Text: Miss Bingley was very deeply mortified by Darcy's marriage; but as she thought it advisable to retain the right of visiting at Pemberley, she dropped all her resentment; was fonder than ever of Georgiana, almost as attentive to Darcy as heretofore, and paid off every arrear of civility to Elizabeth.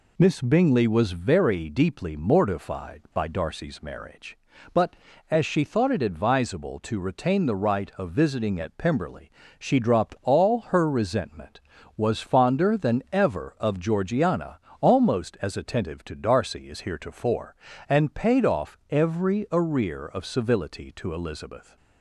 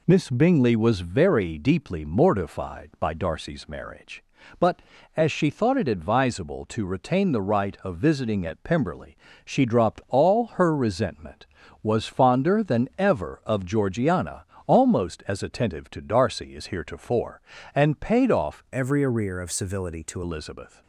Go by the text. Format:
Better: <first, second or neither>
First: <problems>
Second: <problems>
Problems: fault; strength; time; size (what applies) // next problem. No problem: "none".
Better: first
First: none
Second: changes voice from "every" to "to"; from 18.7 to 20.2 s; 1.5 s long